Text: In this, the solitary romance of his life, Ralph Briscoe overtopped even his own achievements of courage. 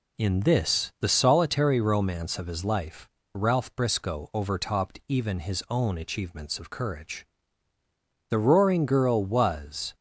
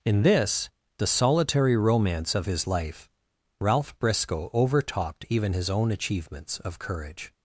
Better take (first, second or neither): second